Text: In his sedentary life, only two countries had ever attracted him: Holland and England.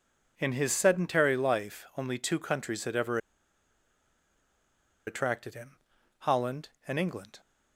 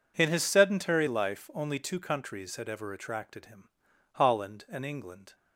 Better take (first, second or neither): second